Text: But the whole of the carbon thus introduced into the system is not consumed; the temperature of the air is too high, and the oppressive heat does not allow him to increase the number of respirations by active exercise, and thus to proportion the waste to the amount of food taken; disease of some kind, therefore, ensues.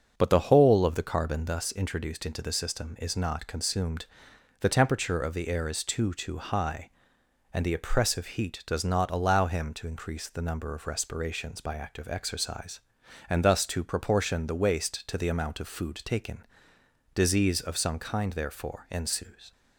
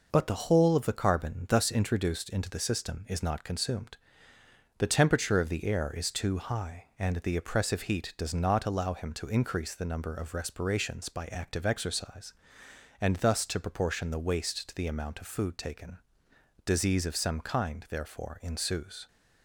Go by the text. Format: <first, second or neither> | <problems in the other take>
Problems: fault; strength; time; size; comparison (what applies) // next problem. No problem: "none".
second | starts louder than the rest; until 1.1 s; 6.5 dB // says "too" twice; at 6.1 s